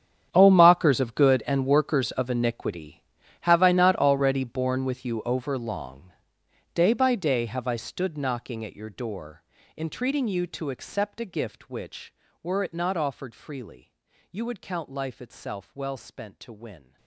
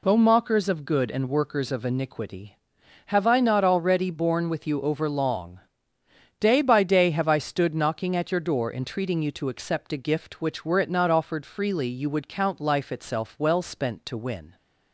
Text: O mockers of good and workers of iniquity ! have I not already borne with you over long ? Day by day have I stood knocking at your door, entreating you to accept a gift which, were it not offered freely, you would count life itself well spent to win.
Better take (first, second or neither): second